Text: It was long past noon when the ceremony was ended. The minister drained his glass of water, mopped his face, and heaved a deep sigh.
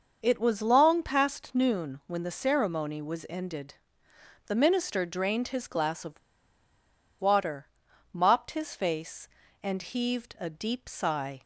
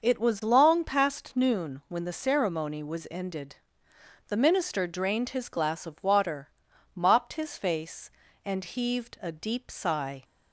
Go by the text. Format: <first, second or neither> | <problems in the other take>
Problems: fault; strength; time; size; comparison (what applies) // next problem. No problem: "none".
second | starts louder than the rest; until 1.2 s; 6.5 dB; also in the second // pauses between "of" and "water"; at 6.1 s; 1.0 s long